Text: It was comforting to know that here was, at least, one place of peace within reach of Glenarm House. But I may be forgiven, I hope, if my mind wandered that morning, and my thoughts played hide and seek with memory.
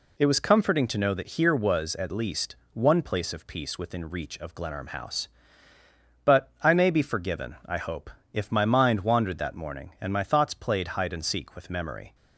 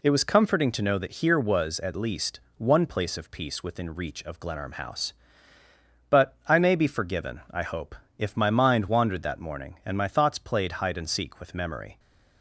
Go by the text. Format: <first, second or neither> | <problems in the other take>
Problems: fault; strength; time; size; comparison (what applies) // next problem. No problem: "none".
neither | none